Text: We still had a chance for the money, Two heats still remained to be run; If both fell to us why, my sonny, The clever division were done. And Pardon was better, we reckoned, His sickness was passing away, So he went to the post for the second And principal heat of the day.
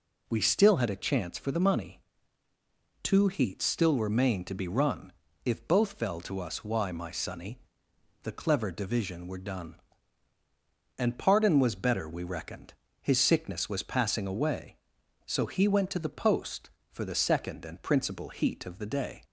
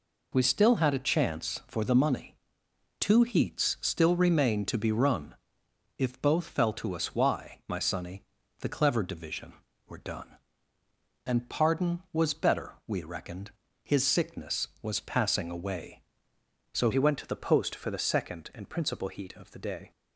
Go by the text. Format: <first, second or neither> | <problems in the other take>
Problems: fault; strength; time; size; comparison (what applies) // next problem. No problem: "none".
first | changes voice at "he"; from 16.9 s on; 3.0 s long